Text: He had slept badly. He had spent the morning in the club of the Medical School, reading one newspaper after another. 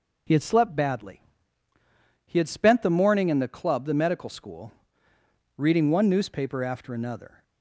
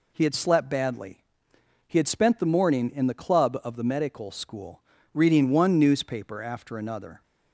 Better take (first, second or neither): second